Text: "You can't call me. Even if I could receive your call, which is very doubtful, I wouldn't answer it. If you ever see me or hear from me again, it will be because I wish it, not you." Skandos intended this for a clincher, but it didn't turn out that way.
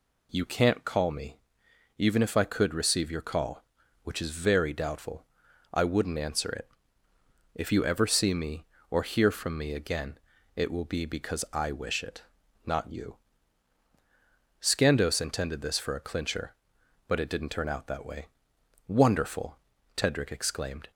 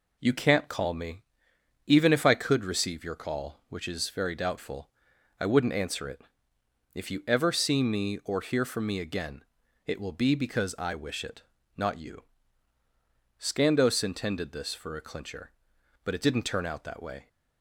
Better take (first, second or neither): second